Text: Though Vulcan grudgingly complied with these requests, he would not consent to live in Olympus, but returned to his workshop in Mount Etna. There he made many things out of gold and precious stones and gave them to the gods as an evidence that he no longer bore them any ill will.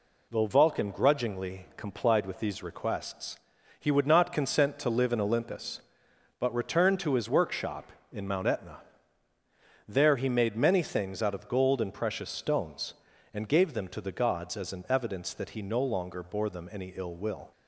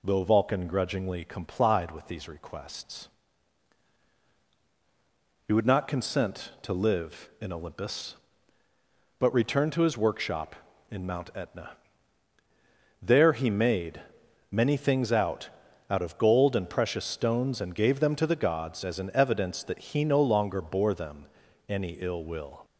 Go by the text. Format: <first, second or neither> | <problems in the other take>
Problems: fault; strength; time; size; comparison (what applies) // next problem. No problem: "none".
first | pauses between "made" and "many"; noticeable; at 13.9 s; 0.50 s long // says "out" twice; at 15.8 s // pauses between "them" and "any"; at 21.2 s; 0.42 s long